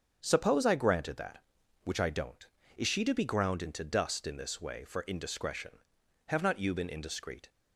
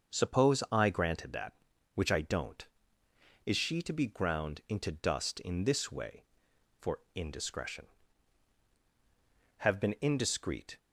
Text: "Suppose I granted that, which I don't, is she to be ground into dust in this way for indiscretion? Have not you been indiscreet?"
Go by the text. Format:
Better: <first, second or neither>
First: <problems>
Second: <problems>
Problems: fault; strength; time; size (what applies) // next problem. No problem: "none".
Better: first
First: starts louder than the rest; strong; until 1.2 s; 7 dB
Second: starts louder than the rest; until 1.2 s; 6.5 dB // pauses between "for" and "indiscretion"; slight; at 6.9 s; 0.16 s long // skips "not you"; at 9.7 s